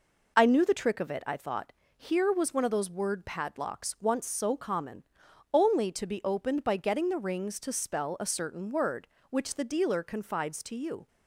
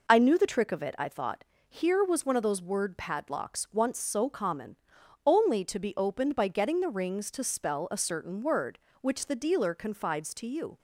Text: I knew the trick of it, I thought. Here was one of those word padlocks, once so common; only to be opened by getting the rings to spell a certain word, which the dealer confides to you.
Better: neither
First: none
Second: none

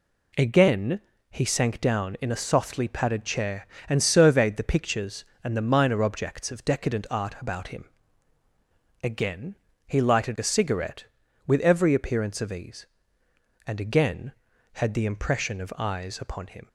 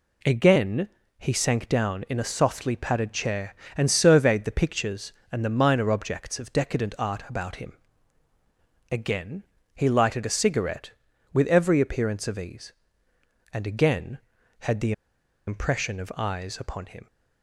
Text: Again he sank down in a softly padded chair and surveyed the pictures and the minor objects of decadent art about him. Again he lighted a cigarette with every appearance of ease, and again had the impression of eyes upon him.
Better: first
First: pauses between "Again" and "he"; slight; at 0.9 s; 0.30 s long // pauses between "Again" and "he"; slight; at 9.5 s; 0.32 s long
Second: pauses between "Again" and "he"; slight; at 0.8 s; 0.30 s long // pauses between "Again" and "he"; slight; at 9.4 s; 0.32 s long // pauses between "the" and "impression"; noticeable; at 14.9 s; 0.55 s long

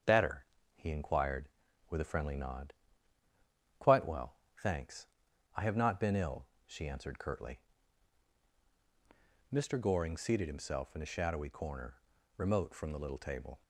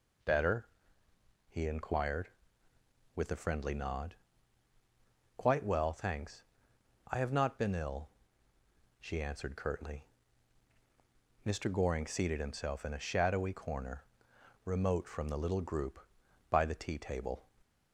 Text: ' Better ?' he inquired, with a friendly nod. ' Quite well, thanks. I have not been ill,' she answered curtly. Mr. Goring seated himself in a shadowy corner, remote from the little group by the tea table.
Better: second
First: starts louder than the rest; until 1.2 s; 7 dB // skips "group by the tea"; at 13.1 s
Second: none

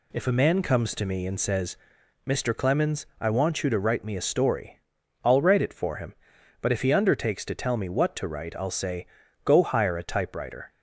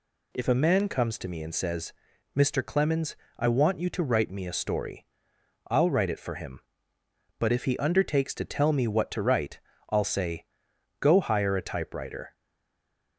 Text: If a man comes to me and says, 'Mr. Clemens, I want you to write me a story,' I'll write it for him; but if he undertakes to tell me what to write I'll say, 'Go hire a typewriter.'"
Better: first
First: none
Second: pauses between "write" and "I'll"; slight; at 9.5 s; 0.30 s long // stays silent after the last word; slight; from 12.3 s on; 0.8 s long

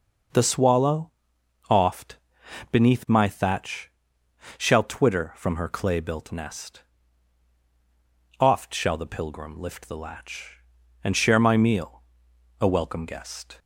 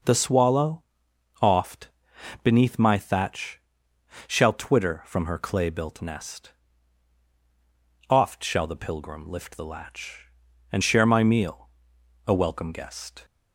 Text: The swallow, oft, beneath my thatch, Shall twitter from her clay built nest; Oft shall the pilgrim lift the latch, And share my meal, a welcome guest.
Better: neither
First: none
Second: none

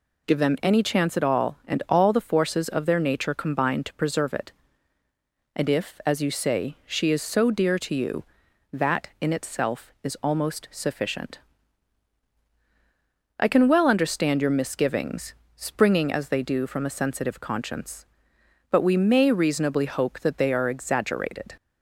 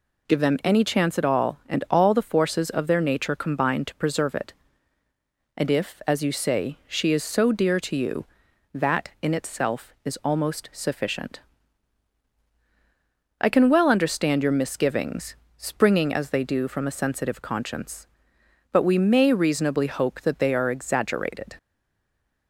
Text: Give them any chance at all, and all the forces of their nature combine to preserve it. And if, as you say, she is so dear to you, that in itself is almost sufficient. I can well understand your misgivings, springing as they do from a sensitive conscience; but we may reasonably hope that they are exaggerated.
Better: first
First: none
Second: stays silent after the last word; slight; from 21.5 s on; 0.9 s long

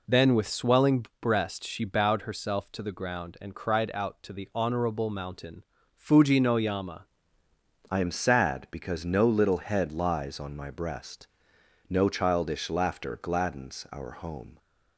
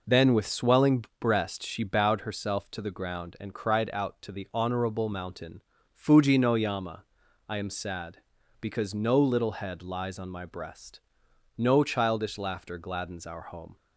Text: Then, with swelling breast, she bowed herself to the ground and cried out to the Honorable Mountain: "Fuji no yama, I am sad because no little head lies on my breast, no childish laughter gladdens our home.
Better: second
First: pauses between "swelling" and "breast"; slight; at 1.0 s; 0.16 s long // changes voice at "I"; from 7.9 s on; 6.6 s long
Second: pauses between "swelling" and "breast"; slight; at 1.0 s; 0.16 s long

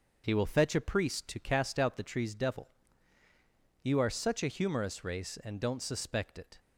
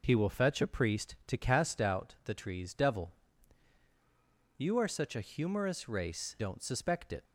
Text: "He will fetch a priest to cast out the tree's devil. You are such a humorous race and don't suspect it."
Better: first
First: none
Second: skips "and"; at 6.3 s

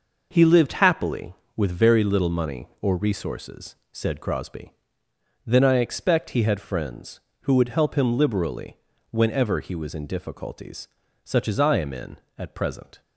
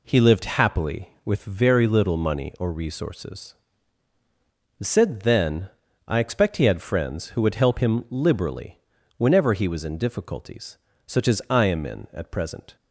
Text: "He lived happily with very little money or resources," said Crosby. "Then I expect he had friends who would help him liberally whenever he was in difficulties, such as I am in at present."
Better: first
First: pauses between "liberally" and "whenever"; slight; at 8.7 s; 0.32 s long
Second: skips "Crosby"; at 5.2 s // pauses between "Then" and "I"; slight; at 5.6 s; 0.36 s long // pauses between "liberally" and "whenever"; slight; at 8.8 s; 0.36 s long

